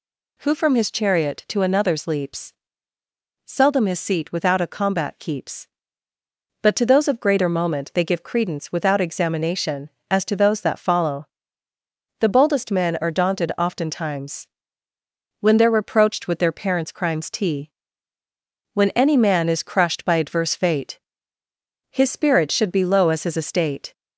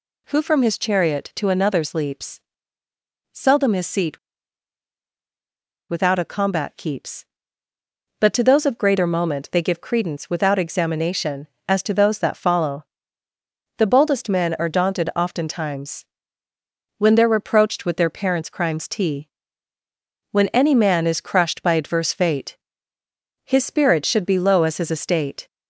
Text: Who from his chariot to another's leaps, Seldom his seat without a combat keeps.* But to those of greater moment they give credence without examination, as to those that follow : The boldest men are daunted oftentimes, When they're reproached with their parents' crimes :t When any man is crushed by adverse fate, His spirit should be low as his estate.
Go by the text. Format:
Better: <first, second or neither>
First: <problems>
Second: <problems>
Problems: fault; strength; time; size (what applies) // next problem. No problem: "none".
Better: first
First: pauses between "t" and "When"; at 17.7 s; 1.0 s long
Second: pauses between "seat" and "without"; strong; at 4.1 s; 1.7 s long // pauses between "t" and "When"; at 19.2 s; 1.0 s long